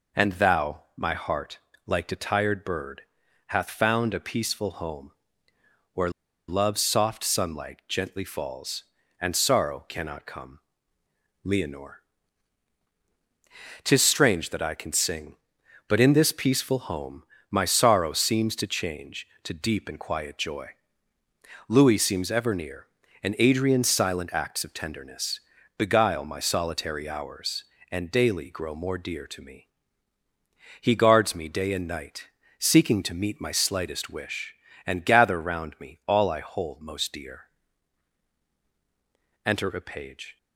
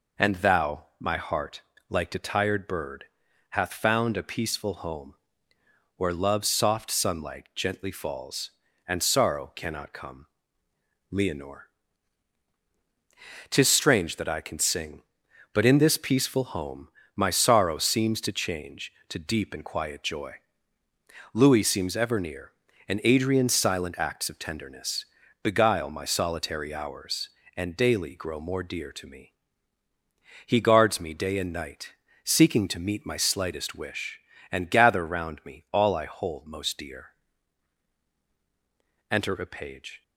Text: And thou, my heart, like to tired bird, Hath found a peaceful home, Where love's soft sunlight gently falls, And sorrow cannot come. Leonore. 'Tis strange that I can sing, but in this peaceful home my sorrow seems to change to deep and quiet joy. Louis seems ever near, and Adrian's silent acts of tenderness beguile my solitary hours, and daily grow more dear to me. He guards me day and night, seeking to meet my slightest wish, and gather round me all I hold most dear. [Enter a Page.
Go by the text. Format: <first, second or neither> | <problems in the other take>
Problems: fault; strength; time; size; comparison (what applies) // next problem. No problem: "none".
second | pauses between "Where" and "love's"; at 6.0 s; 0.39 s long // pauses between "home" and "my"; slight; at 17.2 s; 0.26 s long; slight in the second // pauses between "tenderness" and "beguile"; slight; at 25.3 s; 0.36 s long; slight in the second